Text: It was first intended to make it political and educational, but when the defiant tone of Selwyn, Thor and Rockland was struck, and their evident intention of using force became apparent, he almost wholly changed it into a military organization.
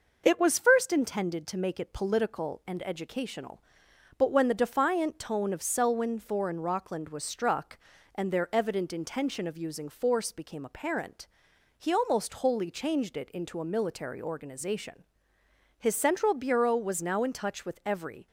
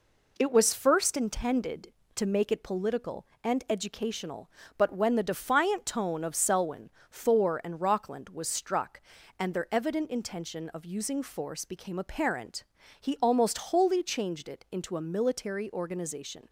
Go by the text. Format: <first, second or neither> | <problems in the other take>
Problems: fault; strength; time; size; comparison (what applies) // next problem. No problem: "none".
second | goes on to say "His central bureau was now in touch with every"; strong; from 15.7 s on; 2.5 s long